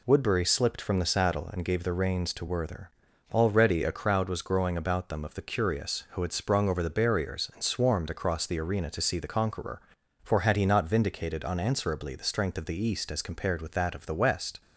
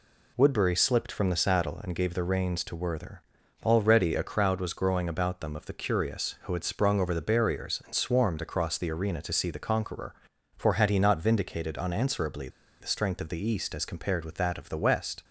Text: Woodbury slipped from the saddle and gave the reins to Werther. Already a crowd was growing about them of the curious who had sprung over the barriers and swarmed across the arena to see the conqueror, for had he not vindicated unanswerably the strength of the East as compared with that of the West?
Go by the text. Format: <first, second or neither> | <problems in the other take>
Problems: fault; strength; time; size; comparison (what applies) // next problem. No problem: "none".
first | pauses between "unanswerably" and "the"; slight; at 12.4 s; 0.32 s long